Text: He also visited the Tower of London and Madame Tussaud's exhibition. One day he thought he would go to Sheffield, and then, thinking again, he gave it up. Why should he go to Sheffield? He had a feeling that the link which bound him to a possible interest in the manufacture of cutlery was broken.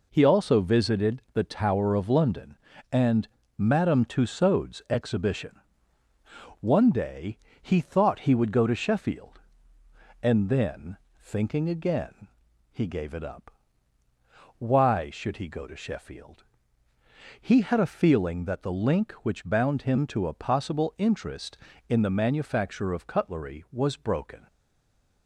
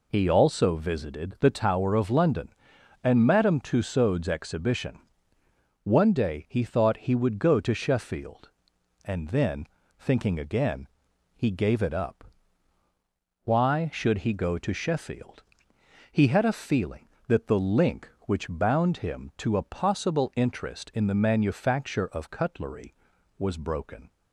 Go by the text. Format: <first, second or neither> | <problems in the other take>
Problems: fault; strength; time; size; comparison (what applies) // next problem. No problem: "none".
second | pauses between "and" and "Madame"; slight; at 3.2 s; 0.30 s long // pauses between "day" and "he"; slight; at 7.3 s; 0.24 s long // stays silent after the last word; slight; from 24.4 s on; 0.8 s long